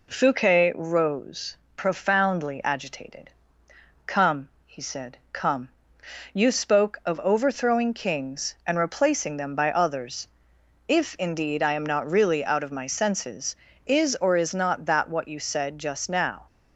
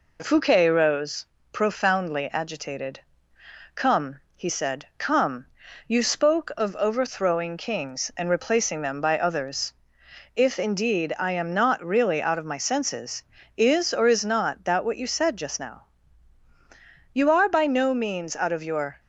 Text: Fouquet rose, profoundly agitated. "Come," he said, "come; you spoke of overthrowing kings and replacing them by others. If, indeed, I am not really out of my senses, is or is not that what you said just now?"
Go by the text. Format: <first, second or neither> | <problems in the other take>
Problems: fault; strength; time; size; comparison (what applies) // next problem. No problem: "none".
first | goes on to say "You are by no means out of your"; strong; from 17.1 s on; 1.8 s long